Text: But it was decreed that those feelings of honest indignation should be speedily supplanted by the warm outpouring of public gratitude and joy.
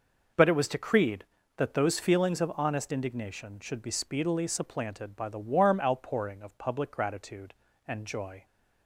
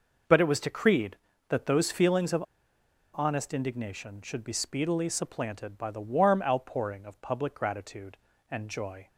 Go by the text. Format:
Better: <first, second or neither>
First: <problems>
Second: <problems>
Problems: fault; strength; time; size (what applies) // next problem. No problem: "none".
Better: first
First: none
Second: pauses between "of" and "honest"; noticeable; at 2.4 s; 0.72 s long